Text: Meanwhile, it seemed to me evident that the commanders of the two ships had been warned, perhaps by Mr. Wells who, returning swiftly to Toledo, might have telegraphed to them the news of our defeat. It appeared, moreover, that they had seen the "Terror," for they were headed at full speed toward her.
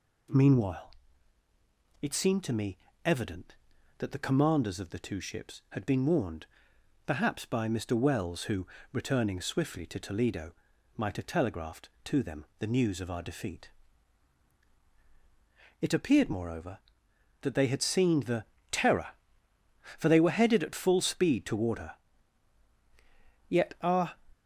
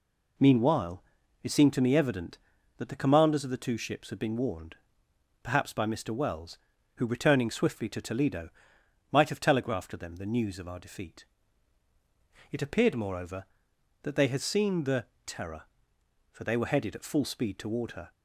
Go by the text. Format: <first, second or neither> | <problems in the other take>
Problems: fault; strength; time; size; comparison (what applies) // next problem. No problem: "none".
second | pauses between "me" and "evident"; slight; at 2.7 s; 0.26 s long // pauses between "the" and "Terror"; slight; at 18.4 s; 0.24 s long; slight in the second // goes on to say "Yet our"; noticeable; from 23.4 s on; 0.64 s long